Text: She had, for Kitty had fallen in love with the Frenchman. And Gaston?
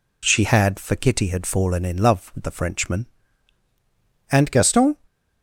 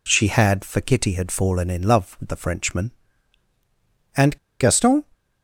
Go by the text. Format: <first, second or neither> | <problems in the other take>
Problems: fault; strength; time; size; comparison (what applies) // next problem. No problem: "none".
first | pauses between "And" and "Gaston"; slight; at 4.3 s; 0.23 s long